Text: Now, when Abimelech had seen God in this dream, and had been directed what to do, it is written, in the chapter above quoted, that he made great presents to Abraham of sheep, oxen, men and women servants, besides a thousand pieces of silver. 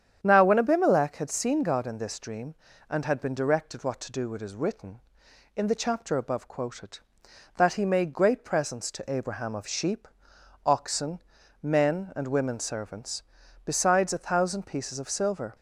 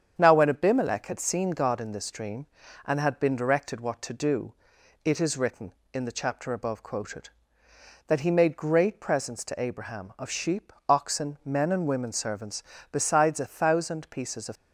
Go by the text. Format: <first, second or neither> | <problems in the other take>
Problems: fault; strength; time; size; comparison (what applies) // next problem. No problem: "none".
first | starts louder than the rest; strong; until 1.1 s; 8 dB; strong in the first // stops before "silver"; at 14.5 s